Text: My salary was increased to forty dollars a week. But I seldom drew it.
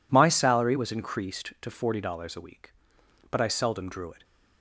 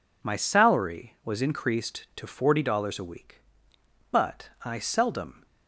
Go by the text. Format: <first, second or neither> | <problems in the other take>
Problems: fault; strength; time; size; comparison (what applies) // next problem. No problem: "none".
first | stops before "drew it"; at 5.4 s